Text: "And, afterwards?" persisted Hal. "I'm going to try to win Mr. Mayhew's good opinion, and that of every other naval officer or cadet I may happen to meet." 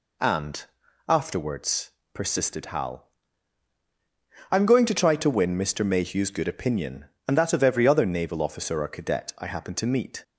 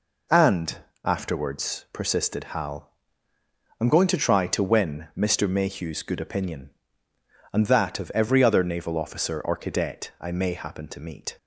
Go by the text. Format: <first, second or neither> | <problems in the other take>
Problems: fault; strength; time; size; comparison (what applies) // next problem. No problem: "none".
second | skips "may"; at 9.4 s